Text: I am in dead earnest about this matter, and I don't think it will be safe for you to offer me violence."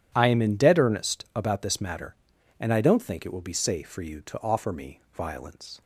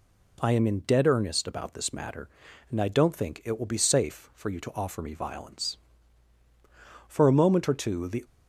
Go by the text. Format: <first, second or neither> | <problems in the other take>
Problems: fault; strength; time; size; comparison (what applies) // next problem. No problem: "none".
first | goes on to say "For a moment or two the"; noticeable; from 7.0 s on; 1.1 s long